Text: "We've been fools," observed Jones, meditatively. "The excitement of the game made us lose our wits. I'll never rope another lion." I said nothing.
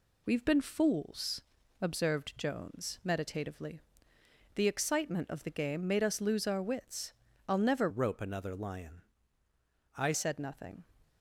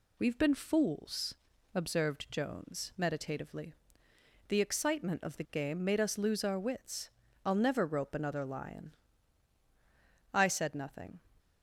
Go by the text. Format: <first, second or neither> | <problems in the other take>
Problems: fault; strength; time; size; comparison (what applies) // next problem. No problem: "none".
second | changes voice from "rope" to "I"; from 7.8 to 10.1 s; 2.3 s long